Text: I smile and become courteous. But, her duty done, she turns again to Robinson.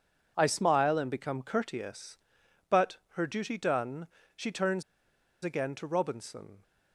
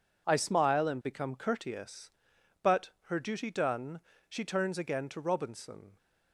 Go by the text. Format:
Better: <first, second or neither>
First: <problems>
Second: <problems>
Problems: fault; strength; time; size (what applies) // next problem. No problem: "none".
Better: second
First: pauses between "turns" and "again"; noticeable; at 4.8 s; 0.61 s long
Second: none